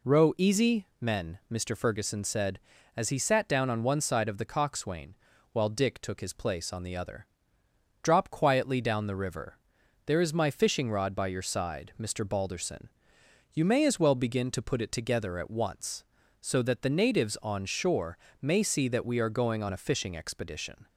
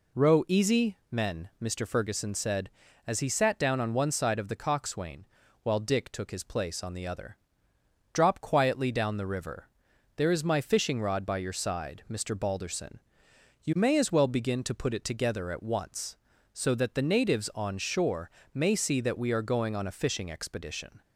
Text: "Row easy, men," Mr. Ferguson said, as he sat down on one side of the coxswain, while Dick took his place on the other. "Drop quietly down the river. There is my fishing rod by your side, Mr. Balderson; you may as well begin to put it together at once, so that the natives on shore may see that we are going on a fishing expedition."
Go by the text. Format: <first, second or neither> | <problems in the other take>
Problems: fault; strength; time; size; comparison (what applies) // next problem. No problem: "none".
neither | pauses between "shore" and "may"; slight; the same in both